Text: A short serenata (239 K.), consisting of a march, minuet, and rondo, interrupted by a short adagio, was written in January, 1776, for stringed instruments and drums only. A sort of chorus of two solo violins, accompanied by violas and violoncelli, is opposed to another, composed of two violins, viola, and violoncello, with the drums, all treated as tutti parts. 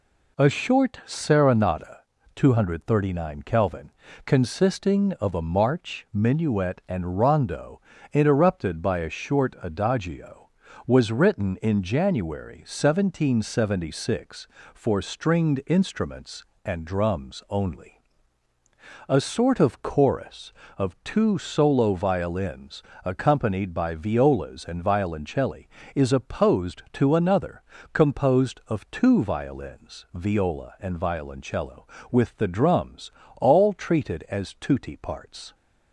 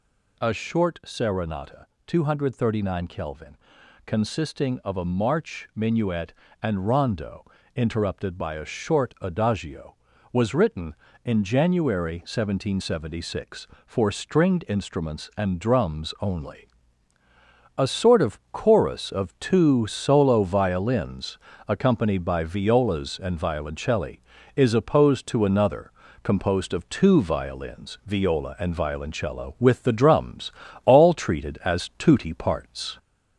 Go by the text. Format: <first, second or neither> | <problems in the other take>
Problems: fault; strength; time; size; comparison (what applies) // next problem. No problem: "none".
first | gets louder; slight; throughout; 2.5 dB